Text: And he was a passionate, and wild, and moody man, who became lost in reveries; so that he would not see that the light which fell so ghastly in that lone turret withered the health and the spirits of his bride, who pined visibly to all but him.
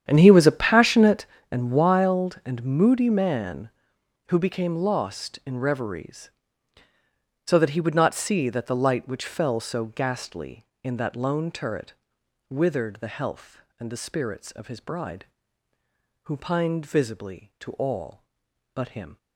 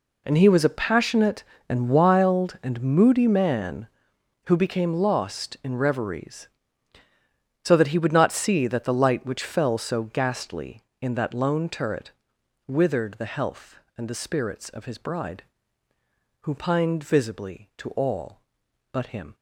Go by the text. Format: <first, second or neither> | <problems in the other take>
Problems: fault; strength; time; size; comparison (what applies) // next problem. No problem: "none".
second | starts louder than the rest; strong; until 1.4 s; 9 dB // pauses between "turret" and "withered"; noticeable; at 11.9 s; 0.56 s long; noticeable in the second